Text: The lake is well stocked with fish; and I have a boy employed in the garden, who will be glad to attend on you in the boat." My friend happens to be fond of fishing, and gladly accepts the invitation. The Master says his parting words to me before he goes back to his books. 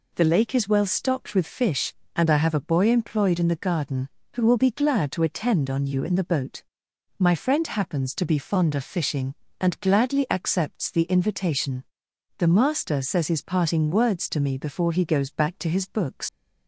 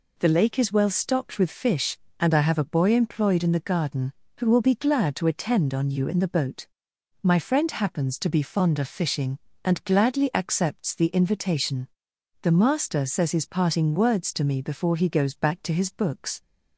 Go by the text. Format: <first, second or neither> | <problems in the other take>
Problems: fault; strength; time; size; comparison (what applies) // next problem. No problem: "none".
second | leaves "books" unfinished; at 16.2 s; 80 ms